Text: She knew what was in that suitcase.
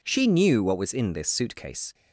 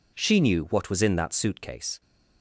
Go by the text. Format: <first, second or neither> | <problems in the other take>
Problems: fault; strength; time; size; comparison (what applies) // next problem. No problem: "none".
second | says "this" for "that"; at 1.1 s